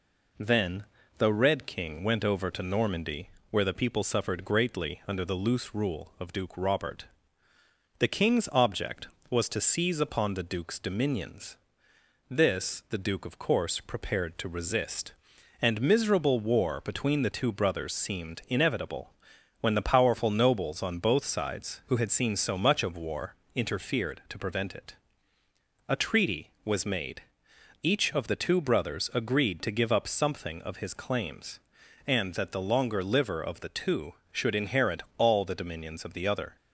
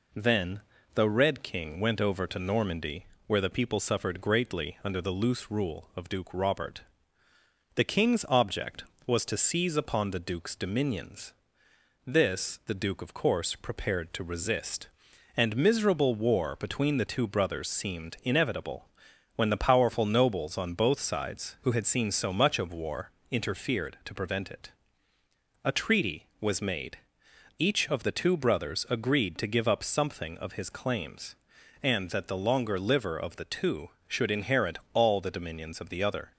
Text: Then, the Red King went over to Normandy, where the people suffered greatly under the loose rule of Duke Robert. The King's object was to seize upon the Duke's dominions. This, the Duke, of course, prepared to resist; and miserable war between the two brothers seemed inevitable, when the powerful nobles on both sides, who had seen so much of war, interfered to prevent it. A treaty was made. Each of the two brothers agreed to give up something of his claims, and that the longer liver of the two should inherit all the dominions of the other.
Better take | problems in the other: neither | pauses between "inherit" and "all"; slight; the same in both

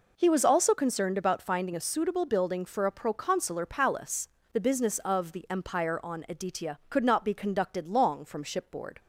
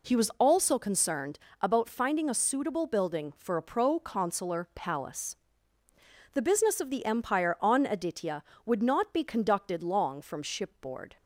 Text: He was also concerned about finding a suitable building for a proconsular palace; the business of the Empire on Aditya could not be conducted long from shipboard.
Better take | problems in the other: first | pauses between "concerned" and "about"; slight; at 1.3 s; 0.22 s long // says "would" for "could"; at 8.6 s

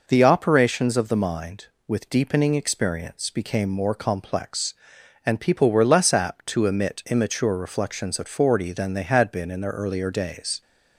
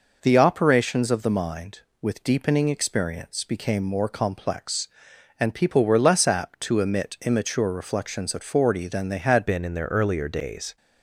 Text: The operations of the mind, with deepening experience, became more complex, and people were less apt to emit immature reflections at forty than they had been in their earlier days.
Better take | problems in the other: first | changes voice at "been"; from 9.4 s on; 1.3 s long

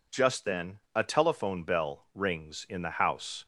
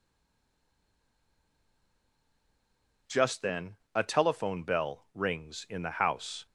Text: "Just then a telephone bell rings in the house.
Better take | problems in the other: first | stays silent before the first word; strong; until 3.0 s; 3.0 s long // pauses between "then" and "a"; slight; at 3.7 s; 0.19 s long; slight in the first

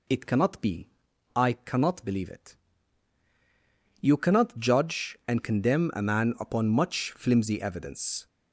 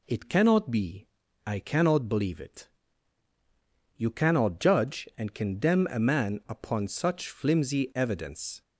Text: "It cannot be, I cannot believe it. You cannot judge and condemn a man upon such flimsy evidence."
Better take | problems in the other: second | says "much" for "such"; at 6.6 s

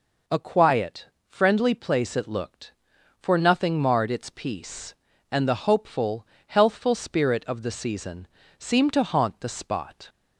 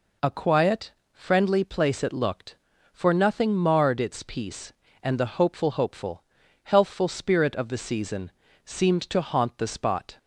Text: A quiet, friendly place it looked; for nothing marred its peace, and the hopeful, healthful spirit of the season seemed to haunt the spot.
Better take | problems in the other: first | says "hopeful" twice; at 5.6 s // pauses between "season" and "seemed"; slight; at 8.3 s; 0.34 s long; slight in the first

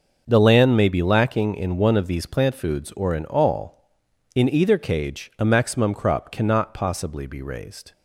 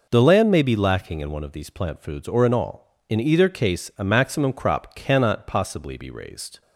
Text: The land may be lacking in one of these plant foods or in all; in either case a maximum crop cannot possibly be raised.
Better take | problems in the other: second | starts louder than the rest; noticeable; until 1.2 s; 6 dB // says "cage" for "case"; at 4.7 s

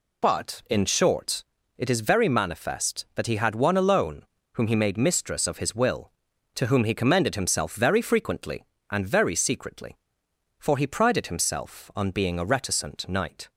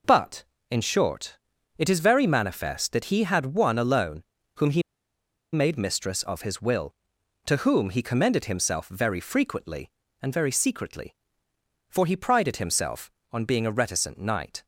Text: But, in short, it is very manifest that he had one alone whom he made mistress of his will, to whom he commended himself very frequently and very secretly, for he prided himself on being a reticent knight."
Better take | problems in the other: first | pauses between "alone" and "whom"; slight; at 4.2 s; 0.32 s long; slight in the first // pauses between "he" and "made"; noticeable; at 4.8 s; 0.72 s long

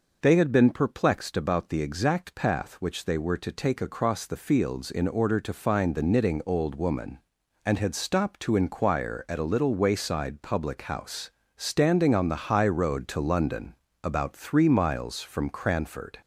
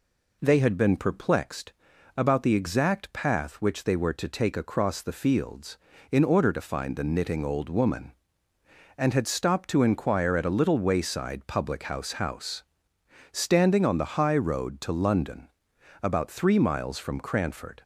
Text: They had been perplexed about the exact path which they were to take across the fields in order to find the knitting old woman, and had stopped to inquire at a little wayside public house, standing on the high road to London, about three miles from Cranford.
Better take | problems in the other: first | pauses between "perplexed" and "about"; at 1.7 s; 0.44 s long // says "house" twice; at 12.1 s

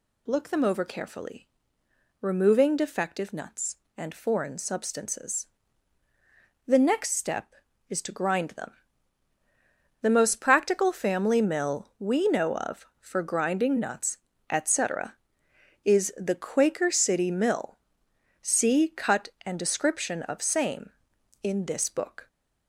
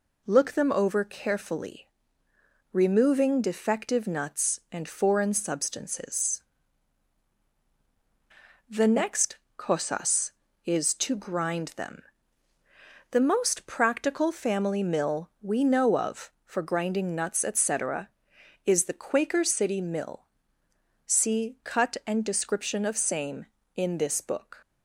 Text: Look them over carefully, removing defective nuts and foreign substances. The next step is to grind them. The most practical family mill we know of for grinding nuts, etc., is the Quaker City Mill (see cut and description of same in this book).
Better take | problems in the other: first | says "cosas" for "step"; at 9.5 s

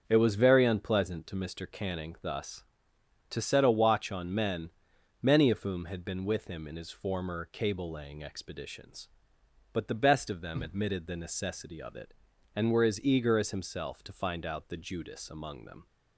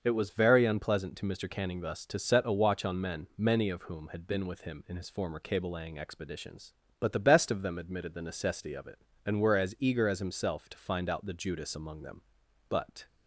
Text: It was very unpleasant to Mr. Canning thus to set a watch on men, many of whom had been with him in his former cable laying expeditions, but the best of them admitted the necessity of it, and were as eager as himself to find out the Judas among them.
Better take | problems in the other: first | starts louder than the rest; noticeable; until 1.0 s; 6 dB; strong in the first // goes on to say "But"; slight; from 12.6 s on; 0.38 s long

